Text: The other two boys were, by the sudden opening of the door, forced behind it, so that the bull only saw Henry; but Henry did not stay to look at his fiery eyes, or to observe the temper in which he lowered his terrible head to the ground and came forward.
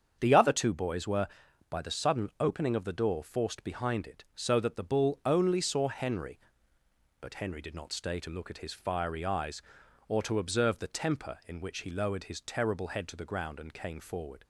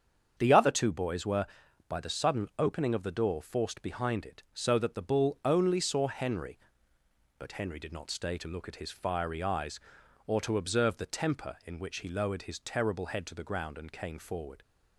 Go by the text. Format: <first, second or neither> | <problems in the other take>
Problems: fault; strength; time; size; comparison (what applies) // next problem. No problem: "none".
neither | starts louder than the rest; strong; the same in both